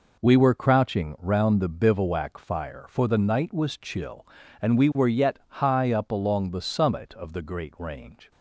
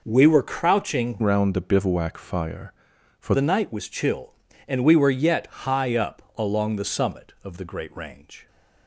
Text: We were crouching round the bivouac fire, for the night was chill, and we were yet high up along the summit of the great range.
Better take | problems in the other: first | changes voice from "round" to "for"; from 1.2 to 3.3 s; 2.1 s long

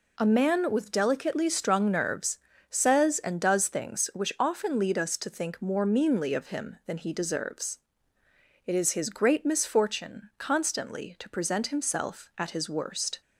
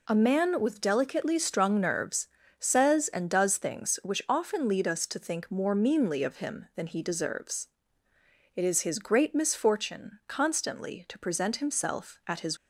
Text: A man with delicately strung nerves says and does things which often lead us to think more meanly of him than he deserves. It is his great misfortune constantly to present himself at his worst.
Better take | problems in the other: first | pauses between "nerves" and "says"; slight; at 2.2 s; 0.32 s long; slight in the first // stops before "worst"; at 12.5 s

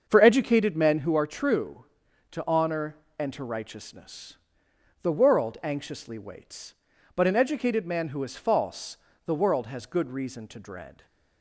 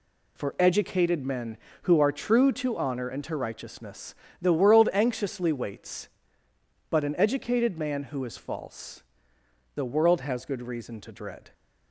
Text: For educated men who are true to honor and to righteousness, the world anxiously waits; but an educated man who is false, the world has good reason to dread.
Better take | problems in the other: second | starts louder than the rest; until 1.2 s; 7 dB

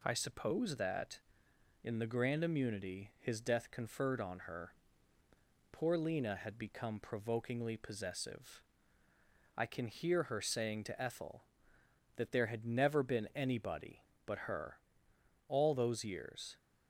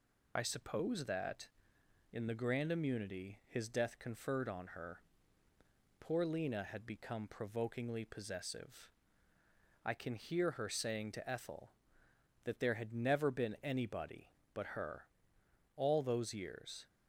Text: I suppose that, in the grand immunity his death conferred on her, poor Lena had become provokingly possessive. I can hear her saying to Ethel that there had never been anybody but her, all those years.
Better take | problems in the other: first | loses the start of "I"; at 0.3 s; 50 ms

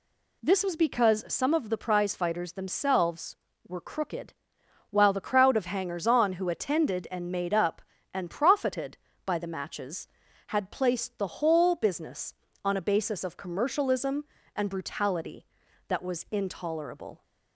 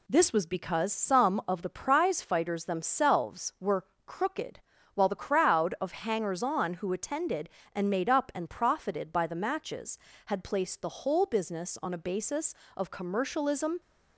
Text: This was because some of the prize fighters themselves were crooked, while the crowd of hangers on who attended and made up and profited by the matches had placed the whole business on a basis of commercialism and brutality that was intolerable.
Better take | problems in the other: first | pauses between "were" and "crooked"; slight; at 3.8 s; 0.22 s long // stops before "and brutality that was intolerable"; at 13.8 s

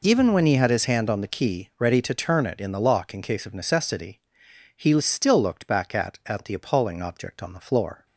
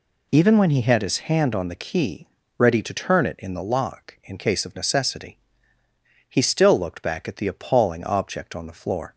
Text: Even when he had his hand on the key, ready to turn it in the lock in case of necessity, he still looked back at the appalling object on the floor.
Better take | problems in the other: second | says "at" twice; at 6.2 s

